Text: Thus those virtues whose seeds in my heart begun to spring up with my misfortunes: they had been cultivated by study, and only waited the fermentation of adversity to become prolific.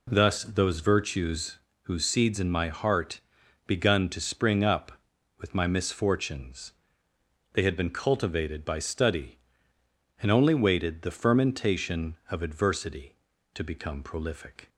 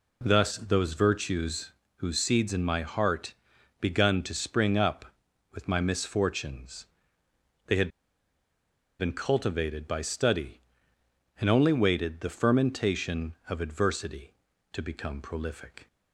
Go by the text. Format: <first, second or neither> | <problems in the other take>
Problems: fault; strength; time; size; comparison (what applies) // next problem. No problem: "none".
first | pauses between "virtues" and "whose"; slight; at 1.7 s; 0.24 s long; slight in the first // pauses between "heart" and "begun"; noticeable; at 3.3 s; 0.46 s long; noticeable in the first // pauses between "had" and "been"; at 7.8 s; 1.0 s long